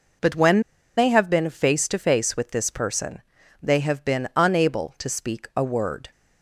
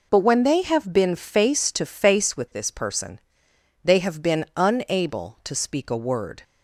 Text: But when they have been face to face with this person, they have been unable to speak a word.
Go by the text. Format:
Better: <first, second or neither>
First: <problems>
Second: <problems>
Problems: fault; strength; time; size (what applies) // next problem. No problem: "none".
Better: second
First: pauses between "when" and "they"; at 0.5 s; 0.37 s long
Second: none